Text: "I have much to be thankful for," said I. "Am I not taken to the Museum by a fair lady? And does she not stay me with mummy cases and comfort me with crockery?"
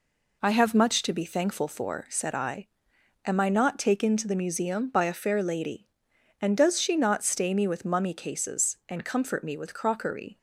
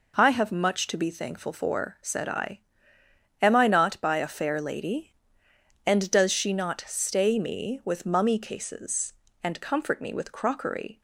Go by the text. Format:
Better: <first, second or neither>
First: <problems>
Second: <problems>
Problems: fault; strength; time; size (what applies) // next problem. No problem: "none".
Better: first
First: none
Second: skips "taken to the Museum"; at 4.0 s